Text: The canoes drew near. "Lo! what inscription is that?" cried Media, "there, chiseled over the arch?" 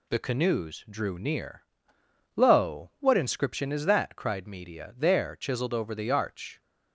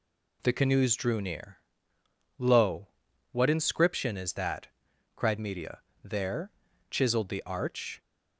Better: first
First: none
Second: skips "over"; at 7.2 s

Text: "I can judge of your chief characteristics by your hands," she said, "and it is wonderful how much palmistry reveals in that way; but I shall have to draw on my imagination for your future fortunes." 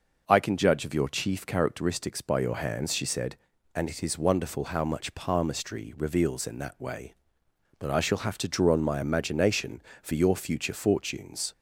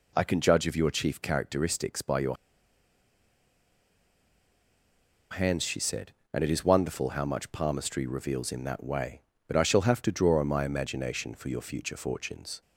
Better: first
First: none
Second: pauses between "your" and "hands"; strong; at 2.3 s; 2.9 s long

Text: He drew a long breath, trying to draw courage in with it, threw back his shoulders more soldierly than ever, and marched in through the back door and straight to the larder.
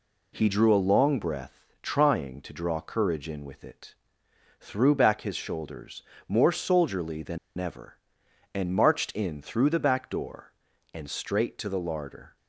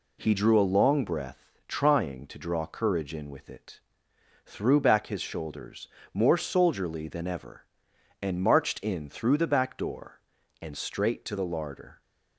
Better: second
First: pauses between "shoulders" and "more"; slight; at 6.0 s; 0.24 s long // pauses between "than" and "ever"; slight; at 7.3 s; 0.19 s long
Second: pauses between "shoulders" and "more"; slight; at 5.8 s; 0.24 s long

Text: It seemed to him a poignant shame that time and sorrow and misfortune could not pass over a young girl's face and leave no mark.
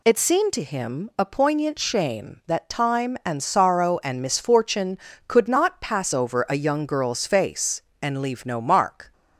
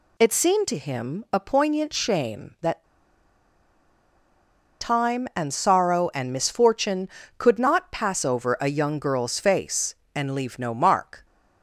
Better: first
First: none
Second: pauses between "that" and "time"; strong; at 2.8 s; 1.9 s long

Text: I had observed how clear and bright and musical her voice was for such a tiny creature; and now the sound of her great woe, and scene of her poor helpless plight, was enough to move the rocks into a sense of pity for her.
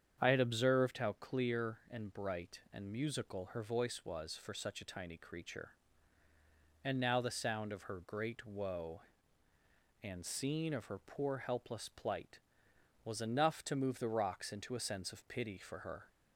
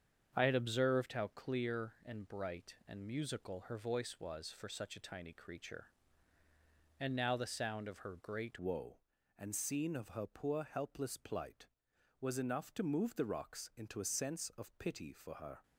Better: first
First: starts louder than the rest; strong; until 1.2 s; 8 dB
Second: starts louder than the rest; strong; until 1.3 s; 7.5 dB // changes voice at "woe"; from 8.5 s on; 7.1 s long

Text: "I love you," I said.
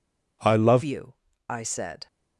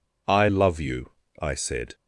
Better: second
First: changes voice at "you"; from 0.8 s on; 1.2 s long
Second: none

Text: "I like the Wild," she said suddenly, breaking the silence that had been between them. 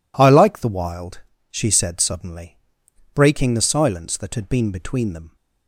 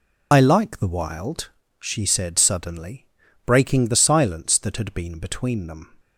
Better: first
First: none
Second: loses the start of "I"; at 0.3 s; 80 ms

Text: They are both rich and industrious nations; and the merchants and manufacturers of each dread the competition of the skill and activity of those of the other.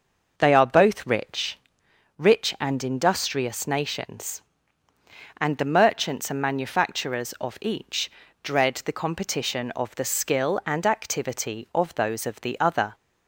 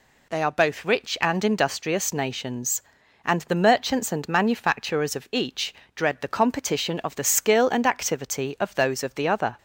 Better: second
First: says "rich" twice; at 2.1 s // pauses between "each" and "dread"; slight; at 8.0 s; 0.32 s long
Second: pauses between "each" and "dread"; slight; at 5.7 s; 0.22 s long

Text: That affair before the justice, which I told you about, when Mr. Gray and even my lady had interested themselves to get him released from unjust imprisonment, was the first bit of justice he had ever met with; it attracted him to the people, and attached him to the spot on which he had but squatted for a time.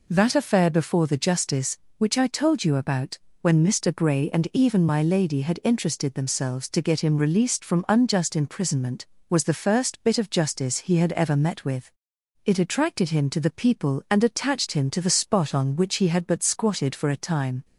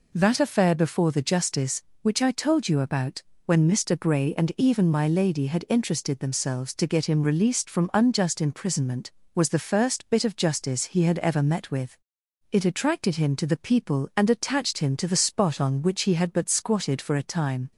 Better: neither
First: none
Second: none

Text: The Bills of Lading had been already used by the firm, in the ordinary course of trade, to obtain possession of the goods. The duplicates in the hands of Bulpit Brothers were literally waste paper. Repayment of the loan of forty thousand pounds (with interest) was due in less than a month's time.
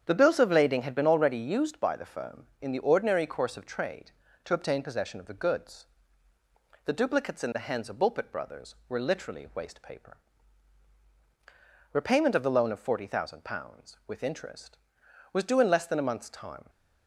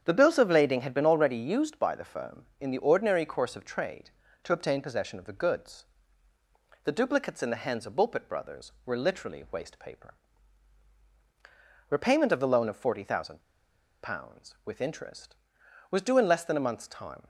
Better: first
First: starts louder than the rest; strong; until 1.0 s; 8 dB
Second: starts louder than the rest; strong; until 1.0 s; 8 dB // pauses between "thousand" and "pounds"; noticeable; at 13.4 s; 0.62 s long

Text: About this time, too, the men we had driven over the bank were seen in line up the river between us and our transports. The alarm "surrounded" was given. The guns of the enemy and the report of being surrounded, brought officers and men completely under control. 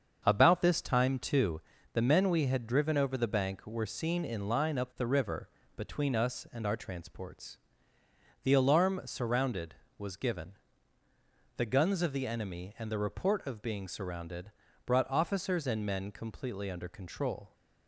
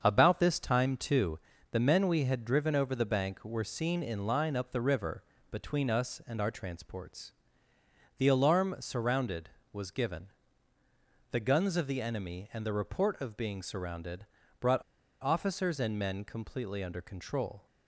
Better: first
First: starts louder than the rest; until 1.2 s; 7 dB // pauses between "river" and "between"; slight; at 5.4 s; 0.30 s long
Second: starts louder than the rest; until 1.0 s; 7 dB // pauses between "river" and "between"; slight; at 5.2 s; 0.30 s long // pauses between "brought" and "officers"; at 14.8 s; 0.39 s long

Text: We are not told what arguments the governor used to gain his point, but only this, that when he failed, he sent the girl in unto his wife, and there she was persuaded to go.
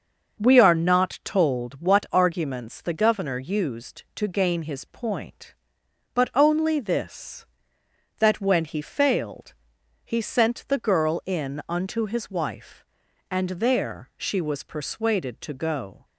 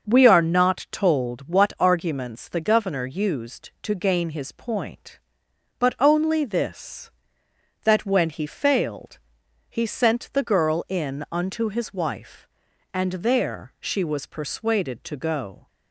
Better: neither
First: starts louder than the rest; noticeable; until 1.4 s; 6 dB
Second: starts louder than the rest; noticeable; until 1.1 s; 6 dB

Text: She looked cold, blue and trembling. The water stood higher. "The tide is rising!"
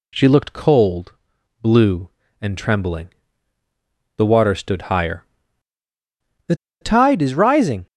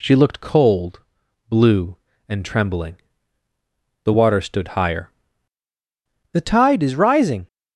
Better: second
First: pauses between "The" and "tide"; slight; at 6.5 s; 0.27 s long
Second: none

